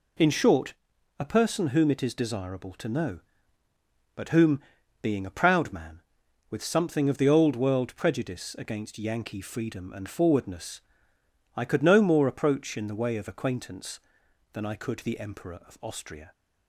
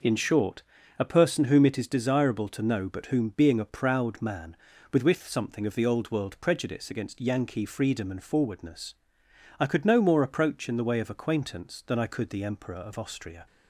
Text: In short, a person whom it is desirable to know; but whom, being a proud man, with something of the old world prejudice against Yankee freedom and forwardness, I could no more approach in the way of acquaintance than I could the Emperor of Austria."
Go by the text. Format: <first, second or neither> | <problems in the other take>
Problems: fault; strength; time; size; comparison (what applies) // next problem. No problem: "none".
first | says "with" twice; at 5.0 s